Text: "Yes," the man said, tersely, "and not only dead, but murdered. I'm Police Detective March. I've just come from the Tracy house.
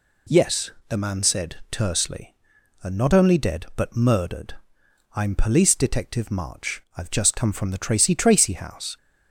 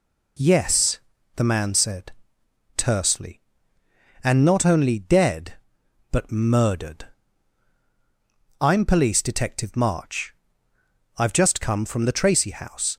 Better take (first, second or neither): second